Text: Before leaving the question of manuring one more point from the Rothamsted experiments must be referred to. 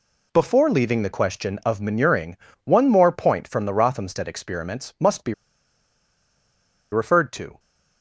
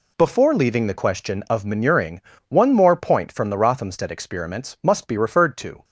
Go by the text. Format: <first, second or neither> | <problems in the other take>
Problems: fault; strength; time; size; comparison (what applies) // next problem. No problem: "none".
second | pauses between "manuring" and "one"; slight; at 2.3 s; 0.26 s long; slight in the second // pauses between "be" and "referred"; strong; at 5.3 s; 1.5 s long